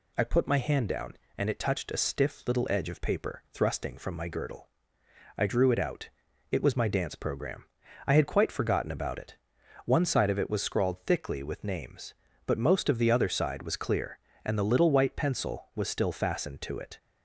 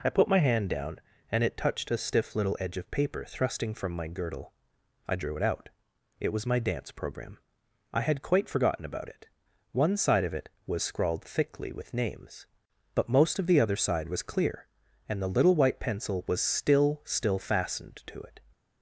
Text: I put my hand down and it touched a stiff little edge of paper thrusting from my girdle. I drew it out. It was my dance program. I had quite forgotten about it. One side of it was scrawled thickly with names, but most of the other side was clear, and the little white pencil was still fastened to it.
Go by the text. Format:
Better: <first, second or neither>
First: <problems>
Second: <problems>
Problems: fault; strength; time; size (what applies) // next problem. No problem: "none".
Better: first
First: none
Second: says "still" twice; at 17.0 s